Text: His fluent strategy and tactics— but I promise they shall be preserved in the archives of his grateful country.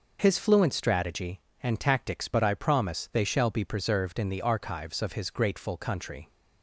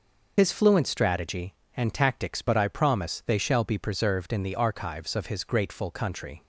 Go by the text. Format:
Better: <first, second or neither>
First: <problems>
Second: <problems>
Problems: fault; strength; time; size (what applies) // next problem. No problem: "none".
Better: first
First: none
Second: loses the start of "His"; at 0.3 s; 50 ms